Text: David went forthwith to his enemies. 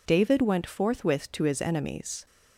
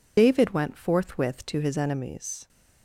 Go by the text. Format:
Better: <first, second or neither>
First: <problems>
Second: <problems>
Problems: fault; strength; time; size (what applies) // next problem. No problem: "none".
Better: first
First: none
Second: loses the start of "David"; at 0.1 s; 70 ms